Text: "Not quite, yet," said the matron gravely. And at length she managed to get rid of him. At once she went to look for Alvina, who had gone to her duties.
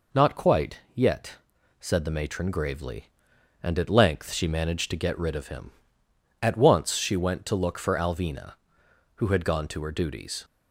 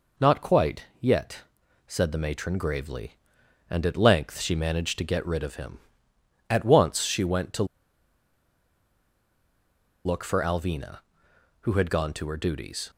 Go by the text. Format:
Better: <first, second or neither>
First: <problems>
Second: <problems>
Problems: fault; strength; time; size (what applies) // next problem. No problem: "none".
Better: first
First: none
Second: pauses between "to" and "look"; strong; at 7.6 s; 2.4 s long